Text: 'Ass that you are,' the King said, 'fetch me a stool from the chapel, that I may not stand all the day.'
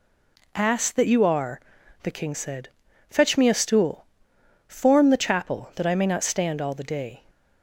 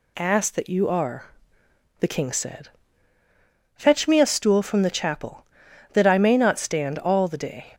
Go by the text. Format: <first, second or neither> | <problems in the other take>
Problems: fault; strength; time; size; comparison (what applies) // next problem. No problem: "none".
second | says "form" for "from"; at 4.6 s